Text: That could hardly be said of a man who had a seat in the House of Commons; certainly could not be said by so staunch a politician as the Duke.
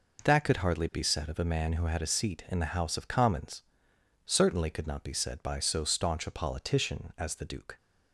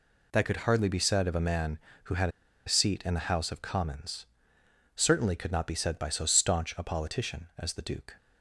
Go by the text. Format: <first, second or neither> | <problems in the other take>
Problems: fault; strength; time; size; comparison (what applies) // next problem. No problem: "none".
first | pauses between "had" and "a"; at 2.2 s; 0.38 s long